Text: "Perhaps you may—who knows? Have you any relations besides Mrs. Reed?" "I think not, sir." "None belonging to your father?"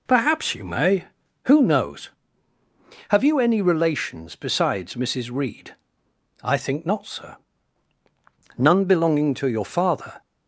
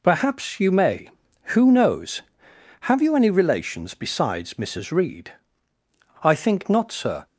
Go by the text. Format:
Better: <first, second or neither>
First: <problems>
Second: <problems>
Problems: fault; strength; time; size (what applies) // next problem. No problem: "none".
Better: first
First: none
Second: stops before "None belonging to your father"; at 7.2 s